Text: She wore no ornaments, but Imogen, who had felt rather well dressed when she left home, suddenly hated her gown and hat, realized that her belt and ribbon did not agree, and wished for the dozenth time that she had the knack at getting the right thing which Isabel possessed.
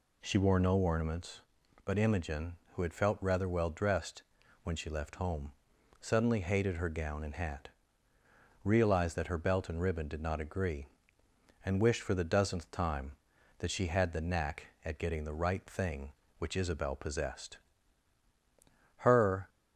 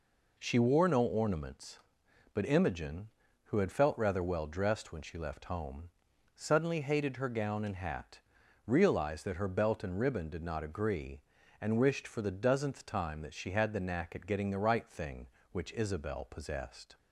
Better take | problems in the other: second | pauses between "dressed" and "when"; at 4.2 s; 0.40 s long // goes on to say "Her"; from 18.9 s on; 0.52 s long

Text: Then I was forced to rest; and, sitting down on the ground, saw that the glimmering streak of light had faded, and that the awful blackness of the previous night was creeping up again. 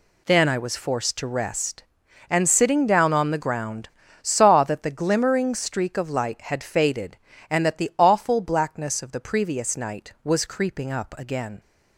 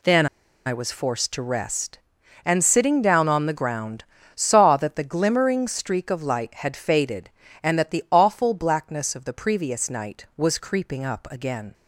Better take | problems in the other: first | pauses between "Then" and "I"; at 0.2 s; 0.40 s long

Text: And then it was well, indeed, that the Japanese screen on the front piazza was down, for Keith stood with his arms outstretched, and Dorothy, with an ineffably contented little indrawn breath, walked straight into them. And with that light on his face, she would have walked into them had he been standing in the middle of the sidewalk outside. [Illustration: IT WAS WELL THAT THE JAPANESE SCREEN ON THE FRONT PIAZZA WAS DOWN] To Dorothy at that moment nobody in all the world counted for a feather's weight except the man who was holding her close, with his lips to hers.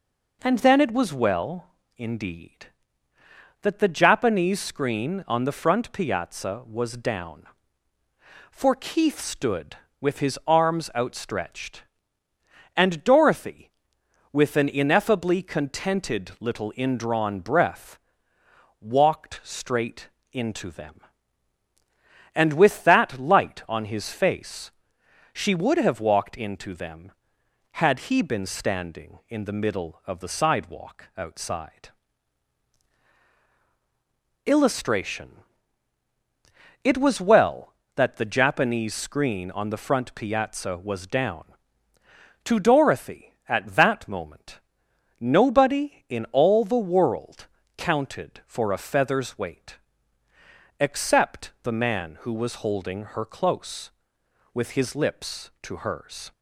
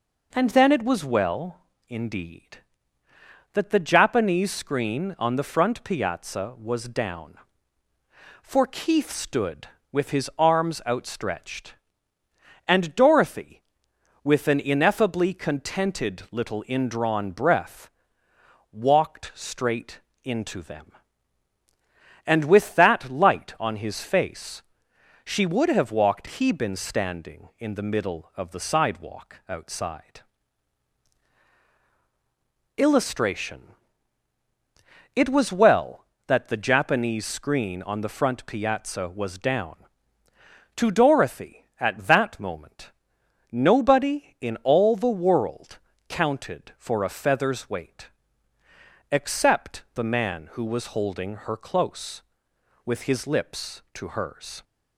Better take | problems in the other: first | pauses between "straight" and "into"; slight; at 19.9 s; 0.24 s long; slight in the first // skips "into them had"; at 26.2 s // pauses between "moment" and "nobody"; noticeable; at 42.9 s; 0.60 s long; noticeable in the first // pauses between "world" and "counted"; slight; at 45.7 s; 0.28 s long; slight in the first // pauses between "weight" and "except"; at 48.0 s; 1.0 s long; also in the first

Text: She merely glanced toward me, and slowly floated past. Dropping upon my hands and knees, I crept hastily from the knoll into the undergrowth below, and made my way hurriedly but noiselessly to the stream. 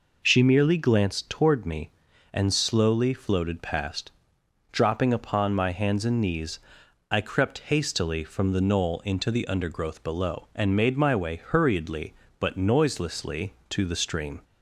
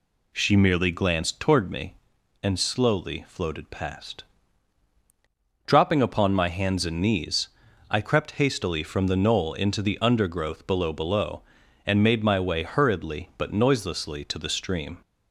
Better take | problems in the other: first | says "below" twice; at 10.9 s

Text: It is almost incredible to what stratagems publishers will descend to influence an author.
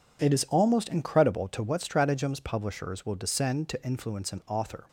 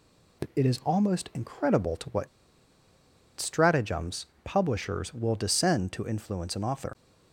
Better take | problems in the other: first | pauses between "what" and "stratagems"; at 2.2 s; 1.1 s long // pauses between "stratagems" and "publishers"; slight; at 4.2 s; 0.18 s long

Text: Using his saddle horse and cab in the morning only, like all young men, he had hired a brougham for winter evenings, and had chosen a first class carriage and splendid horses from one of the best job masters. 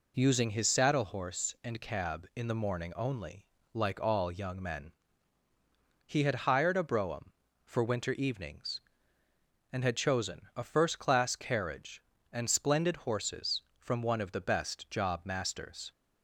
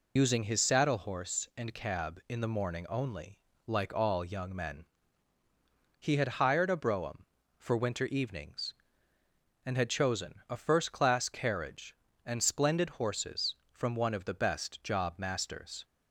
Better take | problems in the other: first | loses the start of "Using"; at 0.1 s; 80 ms

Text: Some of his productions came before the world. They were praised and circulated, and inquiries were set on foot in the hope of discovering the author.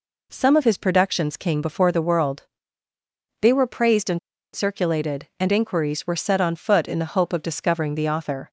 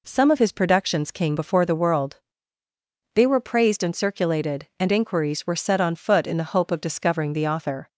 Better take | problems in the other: second | pauses between "and" and "circulated"; slight; at 4.1 s; 0.36 s long

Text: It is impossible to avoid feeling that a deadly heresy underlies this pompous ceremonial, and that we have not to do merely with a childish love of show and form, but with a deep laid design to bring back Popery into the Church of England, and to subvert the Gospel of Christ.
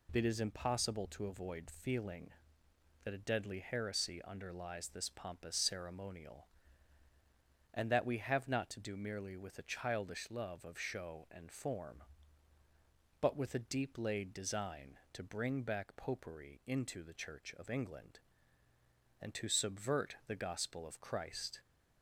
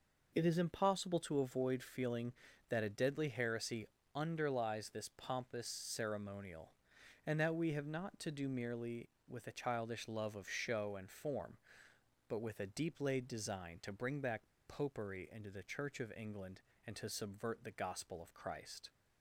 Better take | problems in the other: first | pauses between "heresy" and "underlies"; slight; at 3.8 s; 0.30 s long // pauses between "back" and "Popery"; slight; at 14.4 s; 0.19 s long

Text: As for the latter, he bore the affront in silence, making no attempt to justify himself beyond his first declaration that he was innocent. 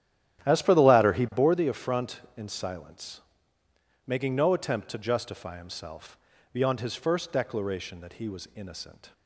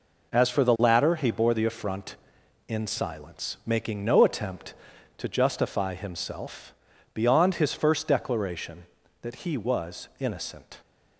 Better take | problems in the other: second | starts louder than the rest; strong; until 1.7 s; 12 dB // pauses between "himself" and "beyond"; slight; at 6.1 s; 0.36 s long; also in the second

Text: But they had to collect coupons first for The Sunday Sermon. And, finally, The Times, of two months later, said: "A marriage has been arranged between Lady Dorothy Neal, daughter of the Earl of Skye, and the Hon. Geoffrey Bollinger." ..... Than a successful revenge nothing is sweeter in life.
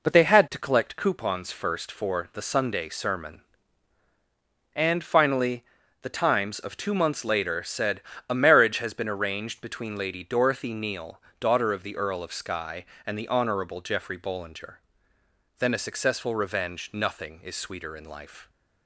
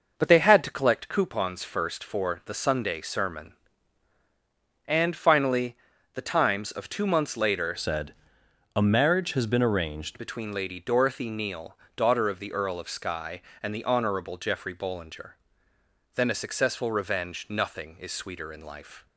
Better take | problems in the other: first | changes voice from "said" to "arranged"; from 7.7 to 10.2 s; 2.5 s long

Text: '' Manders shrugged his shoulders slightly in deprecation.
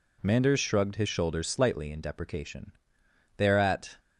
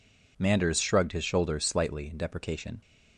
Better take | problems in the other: second | goes on to say "They are at"; from 3.3 s on; 0.58 s long

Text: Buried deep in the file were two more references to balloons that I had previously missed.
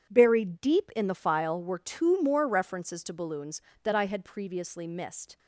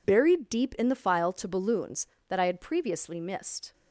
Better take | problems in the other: first | skips "were two more references"; at 1.3 s

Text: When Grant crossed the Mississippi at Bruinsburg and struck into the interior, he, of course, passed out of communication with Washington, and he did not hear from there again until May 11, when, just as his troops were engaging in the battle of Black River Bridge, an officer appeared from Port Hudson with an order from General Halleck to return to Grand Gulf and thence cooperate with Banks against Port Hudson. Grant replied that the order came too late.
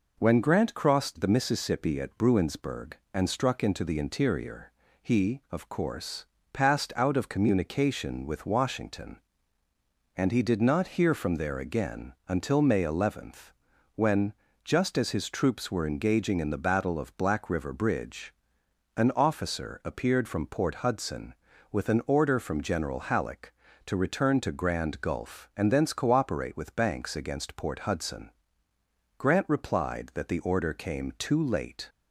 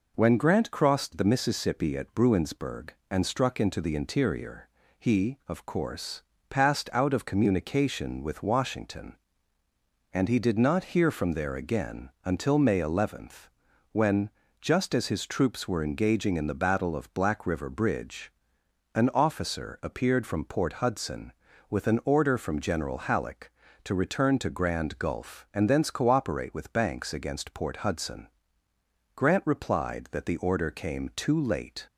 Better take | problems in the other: neither | none

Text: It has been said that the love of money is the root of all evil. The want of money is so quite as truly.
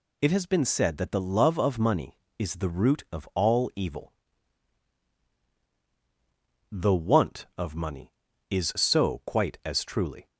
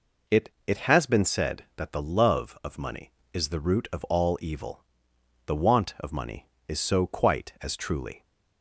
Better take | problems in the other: first | says "It" twice; at 0.6 s

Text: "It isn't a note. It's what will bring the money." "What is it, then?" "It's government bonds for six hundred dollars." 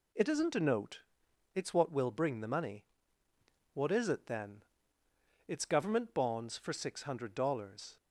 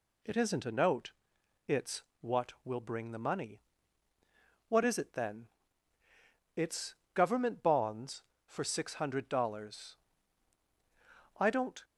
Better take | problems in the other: first | pauses between "It's" and "what"; slight; at 2.0 s; 0.18 s long // pauses between "It's" and "government"; slight; at 6.9 s; 0.20 s long // goes on to say "I don't"; slight; from 11.3 s on; 0.44 s long

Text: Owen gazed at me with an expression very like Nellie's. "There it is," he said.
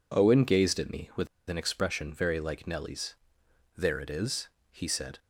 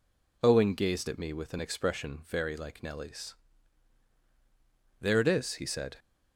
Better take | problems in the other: second | pauses between "with" and "an"; slight; at 1.2 s; 0.22 s long

